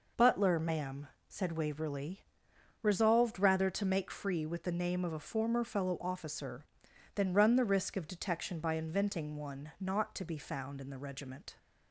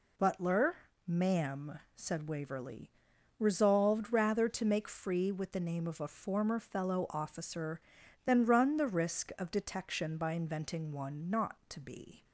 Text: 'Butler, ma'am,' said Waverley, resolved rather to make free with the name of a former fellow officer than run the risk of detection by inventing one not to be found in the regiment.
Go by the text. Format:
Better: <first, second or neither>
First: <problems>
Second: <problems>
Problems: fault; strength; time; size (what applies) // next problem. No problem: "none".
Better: first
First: none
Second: stops before "found in the regiment"; at 12.2 s